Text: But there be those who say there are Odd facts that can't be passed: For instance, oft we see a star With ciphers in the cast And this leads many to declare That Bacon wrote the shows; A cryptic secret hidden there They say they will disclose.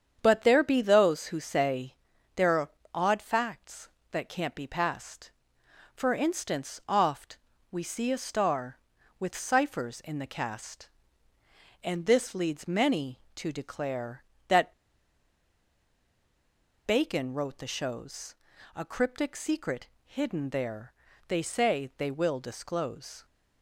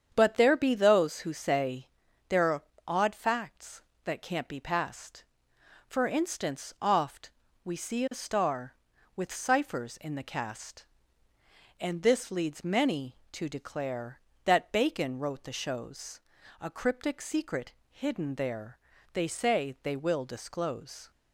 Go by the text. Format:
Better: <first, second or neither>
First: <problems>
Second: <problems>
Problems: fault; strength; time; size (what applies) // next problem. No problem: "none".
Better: second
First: starts louder than the rest; strong; until 1.2 s; 8 dB // pauses between "say" and "there"; at 1.9 s; 0.42 s long // pauses between "are" and "Odd"; slight; at 2.6 s; 0.22 s long // pauses between "oft" and "we"; slight; at 7.3 s; 0.32 s long // pauses between "That" and "Bacon"; strong; at 14.7 s; 2.1 s long // pauses between "secret" and "hidden"; slight; at 19.8 s; 0.18 s long // pauses between "there" and "They"; slight; at 20.9 s; 0.34 s long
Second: starts louder than the rest; strong; until 1.1 s; 8 dB // pauses between "say" and "there"; at 1.8 s; 0.42 s long // pauses between "are" and "Odd"; slight; at 2.6 s; 0.22 s long // pauses between "oft" and "we"; slight; at 7.3 s; 0.32 s long // pauses between "secret" and "hidden"; slight; at 17.7 s; 0.18 s long // pauses between "there" and "They"; slight; at 18.7 s; 0.34 s long